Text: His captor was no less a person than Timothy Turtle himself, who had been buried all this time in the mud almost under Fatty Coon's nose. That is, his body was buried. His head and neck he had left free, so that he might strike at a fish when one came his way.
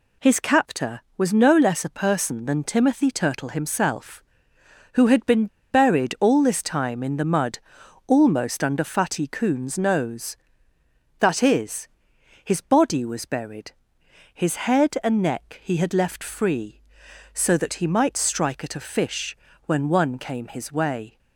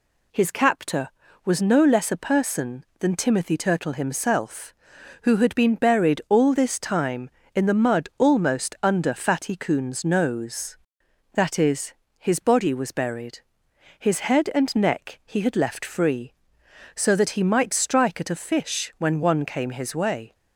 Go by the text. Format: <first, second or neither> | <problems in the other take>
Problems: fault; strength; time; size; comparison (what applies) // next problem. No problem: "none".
second | pauses between "been" and "buried"; slight; at 5.4 s; 0.24 s long // pauses between "mud" and "almost"; noticeable; at 7.5 s; 0.48 s long // pauses between "fish" and "when"; slight; at 19.3 s; 0.30 s long